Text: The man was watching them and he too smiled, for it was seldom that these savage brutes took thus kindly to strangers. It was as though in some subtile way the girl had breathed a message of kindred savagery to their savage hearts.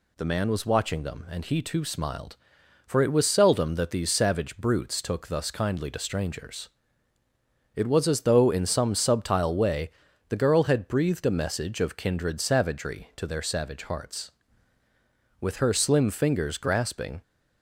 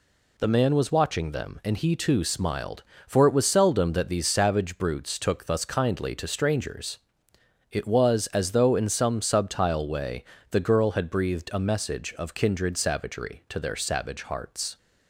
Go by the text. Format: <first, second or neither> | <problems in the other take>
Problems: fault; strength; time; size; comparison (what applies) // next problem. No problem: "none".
second | pauses between "way" and "the"; at 9.9 s; 0.38 s long; slight in the second // goes on to say "With her slim fingers grasping"; strong; from 15.4 s on; 1.8 s long